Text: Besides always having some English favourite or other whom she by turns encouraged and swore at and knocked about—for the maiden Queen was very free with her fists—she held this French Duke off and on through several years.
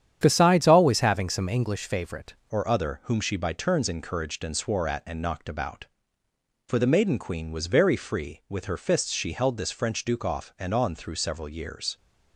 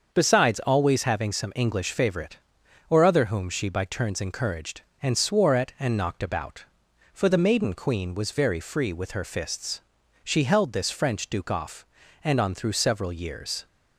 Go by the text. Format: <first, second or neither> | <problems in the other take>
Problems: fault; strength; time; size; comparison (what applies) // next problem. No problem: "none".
second | starts louder than the rest; strong; until 1.2 s; 9 dB; also in the second // changes voice at "or"; from 2.5 s on; 9.4 s long